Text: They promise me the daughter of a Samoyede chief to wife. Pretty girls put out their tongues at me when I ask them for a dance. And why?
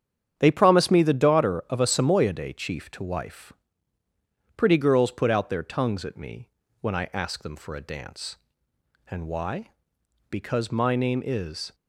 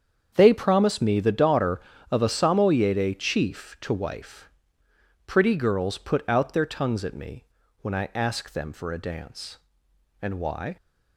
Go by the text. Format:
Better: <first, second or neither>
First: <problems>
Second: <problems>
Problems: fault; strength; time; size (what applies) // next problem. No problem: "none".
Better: second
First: starts louder than the rest; strong; until 1.3 s; 8.5 dB // pauses between "me" and "when"; slight; at 6.4 s; 0.32 s long // goes on to say "Because my name is"; from 10.3 s on; 1.4 s long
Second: starts louder than the rest; strong; until 1.3 s; 7.5 dB // pauses between "me" and "when"; at 7.4 s; 0.38 s long